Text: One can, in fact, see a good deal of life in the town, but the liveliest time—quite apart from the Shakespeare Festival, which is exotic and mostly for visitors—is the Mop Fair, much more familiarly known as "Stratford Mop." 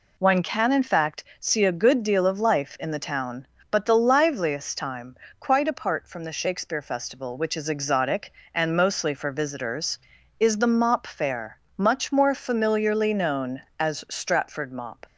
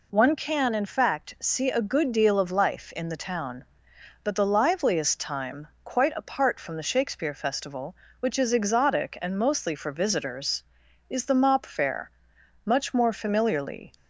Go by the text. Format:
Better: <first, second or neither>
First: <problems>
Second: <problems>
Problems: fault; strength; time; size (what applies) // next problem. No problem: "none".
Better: first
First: none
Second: stops before "known as Stratford Mop"; at 13.9 s